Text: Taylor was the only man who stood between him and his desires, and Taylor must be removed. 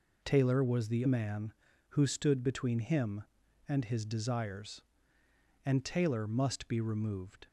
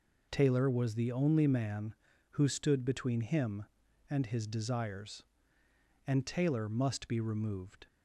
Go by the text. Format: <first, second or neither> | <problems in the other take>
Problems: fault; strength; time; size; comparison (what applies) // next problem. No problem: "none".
second | skips "only"; at 1.0 s